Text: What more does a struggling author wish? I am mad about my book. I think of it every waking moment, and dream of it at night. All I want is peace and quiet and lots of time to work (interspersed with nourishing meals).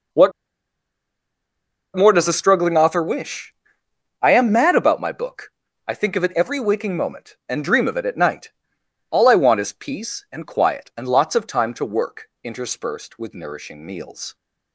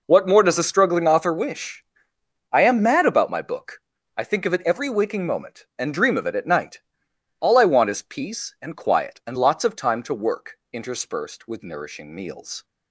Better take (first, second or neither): second